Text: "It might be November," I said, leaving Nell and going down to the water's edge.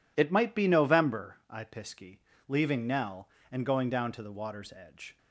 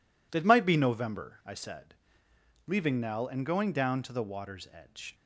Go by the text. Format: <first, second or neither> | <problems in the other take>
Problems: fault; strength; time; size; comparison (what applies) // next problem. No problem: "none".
second | says "pisky" for "said"; at 1.6 s